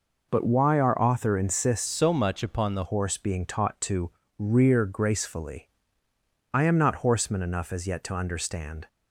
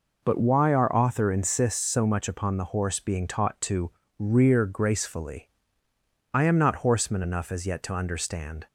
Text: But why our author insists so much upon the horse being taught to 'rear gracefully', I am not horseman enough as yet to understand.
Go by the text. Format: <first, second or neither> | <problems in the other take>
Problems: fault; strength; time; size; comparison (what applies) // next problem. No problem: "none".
second | changes voice from "so" to "the"; from 1.8 to 2.8 s; 1.0 s long // pauses between "to" and "rear"; slight; at 4.0 s; 0.30 s long; slight in the second